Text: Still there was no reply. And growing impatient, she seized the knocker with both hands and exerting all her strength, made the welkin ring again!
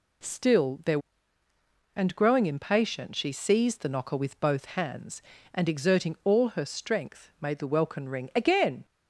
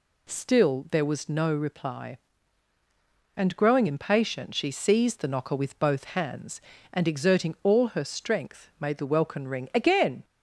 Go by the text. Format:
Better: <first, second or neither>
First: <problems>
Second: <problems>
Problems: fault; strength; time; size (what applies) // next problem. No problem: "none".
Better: second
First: skips "was no reply"; at 1.4 s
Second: none